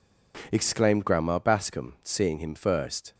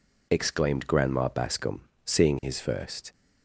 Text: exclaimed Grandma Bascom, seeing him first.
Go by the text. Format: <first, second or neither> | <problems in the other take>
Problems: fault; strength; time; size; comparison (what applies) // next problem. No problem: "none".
first | says "his" for "him"; at 2.4 s